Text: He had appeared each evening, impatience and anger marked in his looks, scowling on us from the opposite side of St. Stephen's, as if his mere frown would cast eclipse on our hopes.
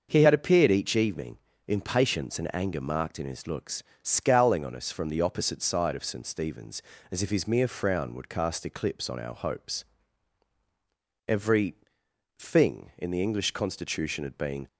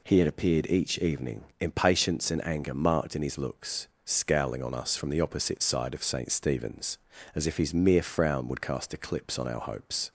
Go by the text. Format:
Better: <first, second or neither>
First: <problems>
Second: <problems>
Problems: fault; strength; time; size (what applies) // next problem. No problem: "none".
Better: second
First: starts louder than the rest; until 1.1 s; 6 dB // goes on to say "Every thing in the English constitution had been"; strong; from 11.2 s on; 3.4 s long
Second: none